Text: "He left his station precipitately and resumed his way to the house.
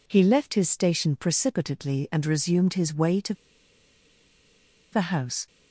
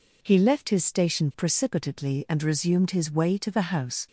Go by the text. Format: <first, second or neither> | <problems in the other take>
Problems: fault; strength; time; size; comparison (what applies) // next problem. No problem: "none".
second | pauses between "to" and "the"; strong; at 3.3 s; 1.5 s long